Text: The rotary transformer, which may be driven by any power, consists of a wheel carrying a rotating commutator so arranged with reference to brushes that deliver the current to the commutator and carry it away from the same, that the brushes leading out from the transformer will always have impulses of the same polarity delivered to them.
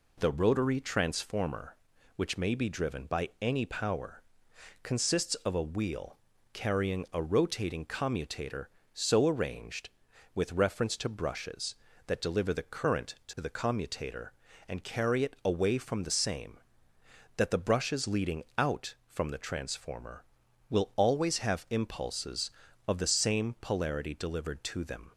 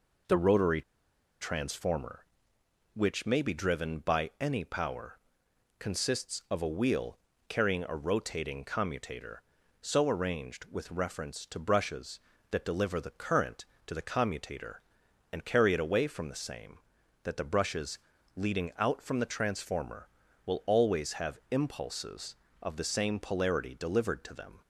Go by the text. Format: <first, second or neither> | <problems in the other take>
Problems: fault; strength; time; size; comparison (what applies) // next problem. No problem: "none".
first | pauses between "rotary" and "transformer"; noticeable; at 0.8 s; 0.59 s long // pauses between "wheel" and "carrying"; slight; at 7.1 s; 0.28 s long; slight in the first // pauses between "brushes" and "leading"; slight; at 17.9 s; 0.36 s long